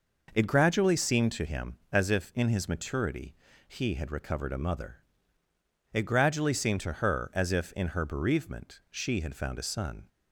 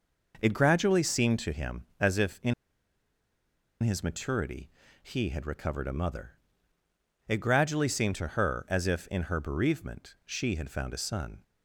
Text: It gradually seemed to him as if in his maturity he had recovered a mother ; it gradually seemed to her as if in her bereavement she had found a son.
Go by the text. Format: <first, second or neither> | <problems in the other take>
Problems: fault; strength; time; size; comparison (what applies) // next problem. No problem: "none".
first | pauses between "in" and "his"; strong; at 2.5 s; 1.2 s long // pauses between "maturity" and "he"; slight; at 4.6 s; 0.34 s long; slight in the first